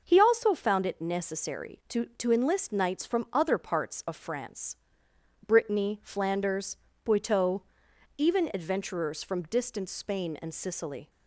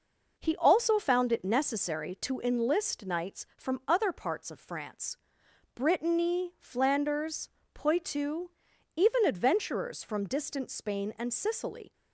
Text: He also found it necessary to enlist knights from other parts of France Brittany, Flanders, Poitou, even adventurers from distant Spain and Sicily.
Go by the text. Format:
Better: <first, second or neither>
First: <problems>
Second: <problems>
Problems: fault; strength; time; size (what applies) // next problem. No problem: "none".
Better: second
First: says "to" twice; at 2.1 s // pauses between "France" and "Brittany"; noticeable; at 4.7 s; 0.70 s long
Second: pauses between "France" and "Brittany"; noticeable; at 5.1 s; 0.58 s long